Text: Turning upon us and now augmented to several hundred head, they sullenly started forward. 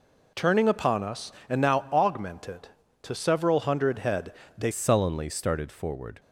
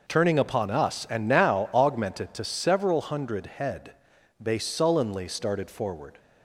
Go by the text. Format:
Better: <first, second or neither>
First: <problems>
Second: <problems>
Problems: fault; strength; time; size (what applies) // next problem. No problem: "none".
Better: second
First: changes voice at "sullenly"; from 4.7 s on; 1.4 s long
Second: none